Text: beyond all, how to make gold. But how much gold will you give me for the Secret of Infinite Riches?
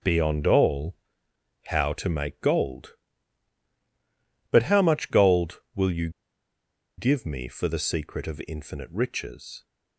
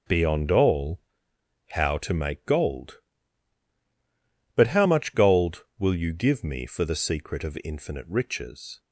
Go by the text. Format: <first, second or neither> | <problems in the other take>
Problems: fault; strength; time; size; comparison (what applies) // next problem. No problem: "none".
second | starts louder than the rest; strong; until 1.7 s; 7 dB; strong in the second // pauses between "you" and "give"; noticeable; at 6.0 s; 0.88 s long